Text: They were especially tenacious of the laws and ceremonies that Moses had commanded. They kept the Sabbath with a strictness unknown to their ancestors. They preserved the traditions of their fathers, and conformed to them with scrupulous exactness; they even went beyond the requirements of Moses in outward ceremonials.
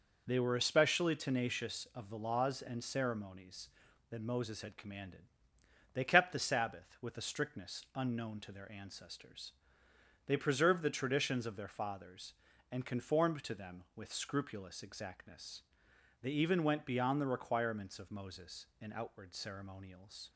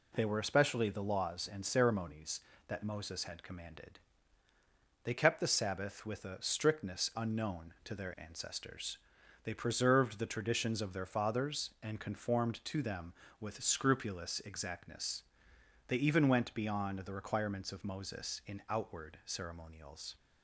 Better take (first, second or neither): first